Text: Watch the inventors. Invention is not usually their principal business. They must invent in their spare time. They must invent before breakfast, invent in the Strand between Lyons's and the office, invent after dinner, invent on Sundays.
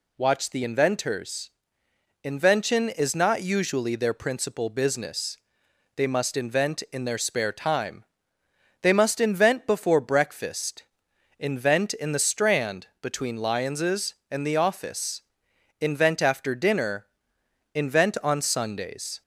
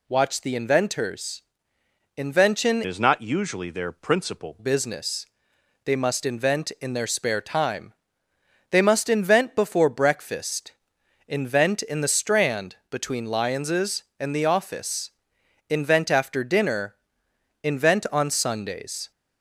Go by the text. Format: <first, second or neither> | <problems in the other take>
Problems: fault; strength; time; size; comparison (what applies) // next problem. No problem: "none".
first | changes voice from "is" to "principal"; from 2.8 to 4.5 s; 1.7 s long